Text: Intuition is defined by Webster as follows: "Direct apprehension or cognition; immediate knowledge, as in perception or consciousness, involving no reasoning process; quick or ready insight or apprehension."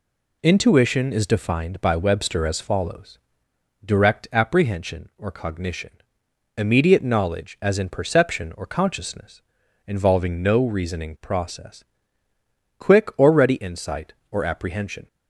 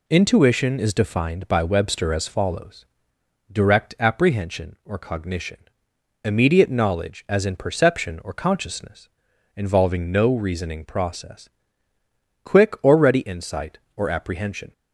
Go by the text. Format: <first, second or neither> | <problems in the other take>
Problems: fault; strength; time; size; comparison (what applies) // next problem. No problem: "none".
neither | none